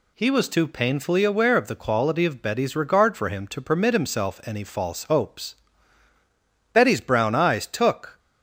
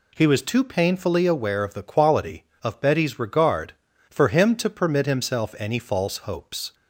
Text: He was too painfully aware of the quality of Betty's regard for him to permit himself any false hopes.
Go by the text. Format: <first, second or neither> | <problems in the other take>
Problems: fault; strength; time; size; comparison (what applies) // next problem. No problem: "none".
second | goes on to say "Betty's brown eyes took"; from 6.7 s on; 1.4 s long